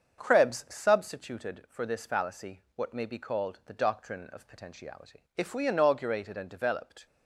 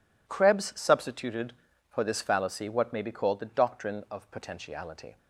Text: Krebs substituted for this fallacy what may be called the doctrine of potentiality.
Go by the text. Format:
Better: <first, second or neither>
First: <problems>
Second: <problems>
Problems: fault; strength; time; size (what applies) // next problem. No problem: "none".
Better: second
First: starts louder than the rest; until 1.2 s; 7 dB // goes on to say "If we inaugurated and developed"; strong; from 5.3 s on; 1.6 s long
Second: none